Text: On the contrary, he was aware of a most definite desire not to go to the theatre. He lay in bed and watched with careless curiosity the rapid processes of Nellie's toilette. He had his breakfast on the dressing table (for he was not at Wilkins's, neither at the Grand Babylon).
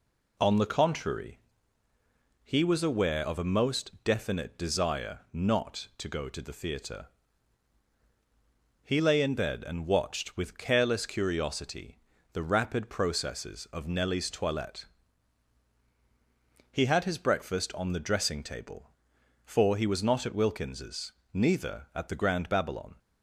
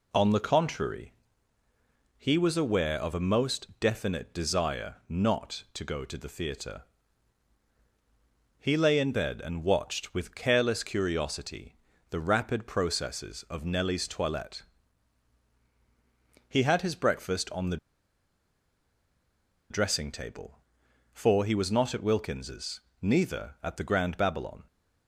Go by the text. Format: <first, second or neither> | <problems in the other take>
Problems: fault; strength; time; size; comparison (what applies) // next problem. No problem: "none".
first | pauses between "curiosity" and "the"; slight; at 11.7 s; 0.32 s long; slight in the first // pauses between "the" and "dressing"; strong; at 17.7 s; 1.9 s long